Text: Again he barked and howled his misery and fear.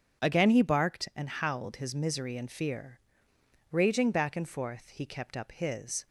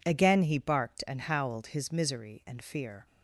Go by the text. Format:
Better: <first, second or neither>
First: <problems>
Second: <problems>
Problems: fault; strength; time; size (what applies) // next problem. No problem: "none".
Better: second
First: starts louder than the rest; strong; until 1.3 s; 7.5 dB // goes on to say "Raging back and forth he kept up his"; strong; from 3.7 s on; 2.3 s long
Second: none